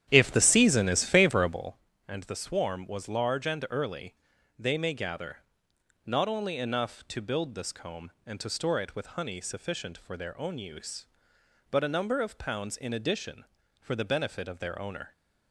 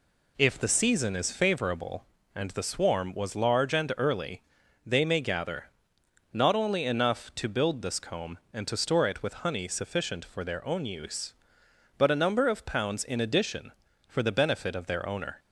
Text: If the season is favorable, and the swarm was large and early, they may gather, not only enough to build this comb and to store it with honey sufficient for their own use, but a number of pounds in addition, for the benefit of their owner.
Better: second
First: starts louder than the rest; strong; until 1.7 s; 10.5 dB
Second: none

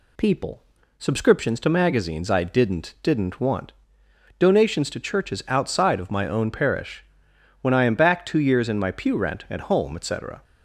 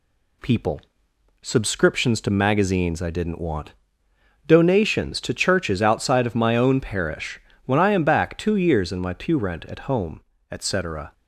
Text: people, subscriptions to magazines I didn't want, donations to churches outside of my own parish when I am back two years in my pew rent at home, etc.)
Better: second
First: says "didn't" twice; at 3.0 s // pauses between "parish" and "when"; noticeable; at 7.0 s; 0.58 s long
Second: pauses between "parish" and "when"; slight; at 7.4 s; 0.24 s long

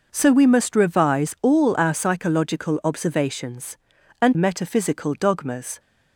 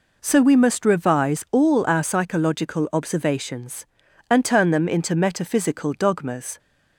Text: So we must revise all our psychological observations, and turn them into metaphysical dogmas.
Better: second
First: skips "turn them into"; at 4.3 s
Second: none

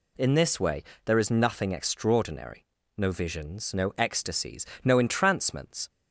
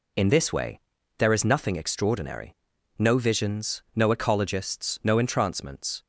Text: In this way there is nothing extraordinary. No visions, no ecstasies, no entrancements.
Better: first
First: pauses between "way" and "there"; slight; at 0.8 s; 0.22 s long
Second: pauses between "way" and "there"; at 0.7 s; 0.40 s long // says "ecologists" for "ecstasies"; at 4.0 s

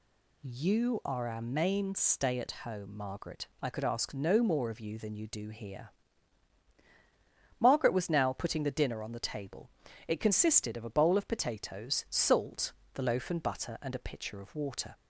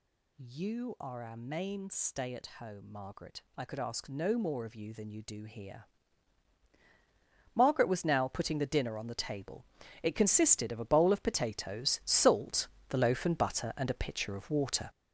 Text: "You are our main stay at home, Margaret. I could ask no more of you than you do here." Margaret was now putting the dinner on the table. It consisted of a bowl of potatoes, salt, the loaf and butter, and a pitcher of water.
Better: first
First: none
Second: gets louder; strong; throughout; 9 dB

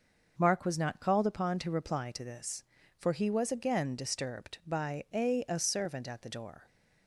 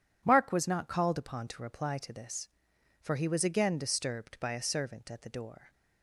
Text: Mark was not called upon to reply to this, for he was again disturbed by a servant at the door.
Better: second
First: says "a" twice; at 5.4 s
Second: none

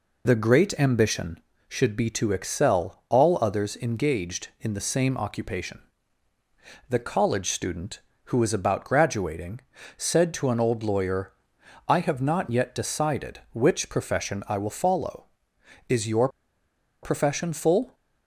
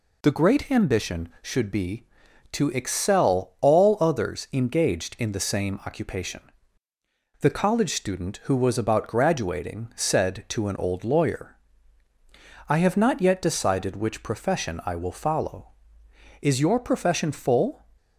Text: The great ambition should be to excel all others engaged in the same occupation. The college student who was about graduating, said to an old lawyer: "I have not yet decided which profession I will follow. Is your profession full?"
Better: second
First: pauses between "your" and "profession"; noticeable; at 16.2 s; 0.74 s long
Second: none

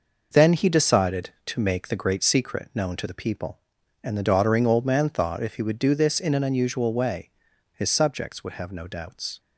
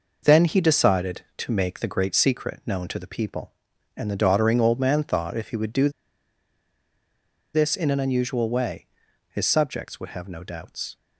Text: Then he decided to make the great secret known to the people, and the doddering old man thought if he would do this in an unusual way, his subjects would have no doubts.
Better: first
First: none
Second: pauses between "do" and "this"; strong; at 5.8 s; 1.6 s long

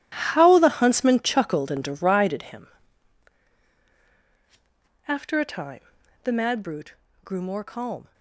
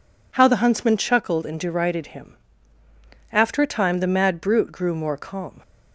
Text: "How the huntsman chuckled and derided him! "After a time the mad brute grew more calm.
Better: second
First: gets quieter; strong; throughout; 13 dB // pauses between "time" and "the"; at 5.8 s; 0.44 s long // pauses between "brute" and "grew"; slight; at 6.9 s; 0.27 s long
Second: none

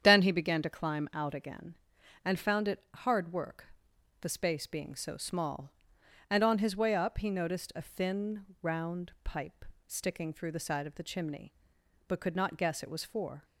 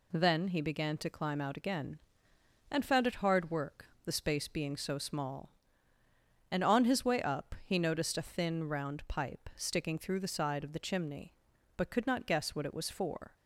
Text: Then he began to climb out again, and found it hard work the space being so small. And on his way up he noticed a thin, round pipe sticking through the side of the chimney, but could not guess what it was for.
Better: second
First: starts louder than the rest; strong; until 1.0 s; 8.5 dB // pauses between "work" and "the"; noticeable; at 3.6 s; 0.54 s long // pauses between "pipe" and "sticking"; slight; at 9.6 s; 0.22 s long // skips "what"; at 12.8 s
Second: pauses between "work" and "the"; slight; at 3.8 s; 0.18 s long

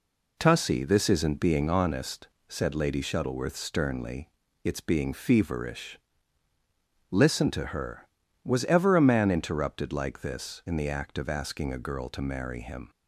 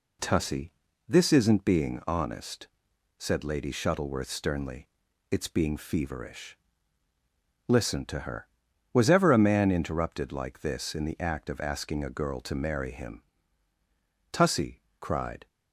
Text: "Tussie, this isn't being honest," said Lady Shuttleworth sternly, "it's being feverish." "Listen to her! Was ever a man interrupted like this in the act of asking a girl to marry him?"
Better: first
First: none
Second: goes on to say "Tussie cried"; noticeable; from 14.3 s on; 1.1 s long

